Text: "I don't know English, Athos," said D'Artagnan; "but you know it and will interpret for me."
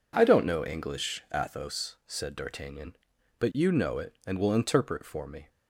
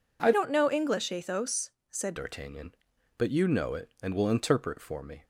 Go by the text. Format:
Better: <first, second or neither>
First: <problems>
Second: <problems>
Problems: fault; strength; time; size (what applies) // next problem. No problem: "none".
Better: first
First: none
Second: changes voice from "don't" to "said"; from 0.3 to 2.1 s; 1.8 s long